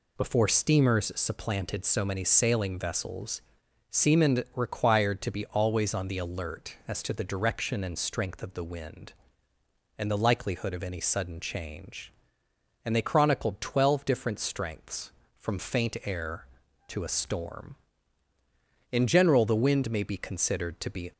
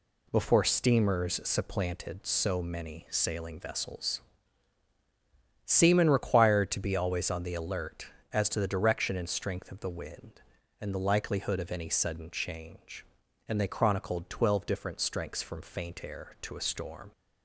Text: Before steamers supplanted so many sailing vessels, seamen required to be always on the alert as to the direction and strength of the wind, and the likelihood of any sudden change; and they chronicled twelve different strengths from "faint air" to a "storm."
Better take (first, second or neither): second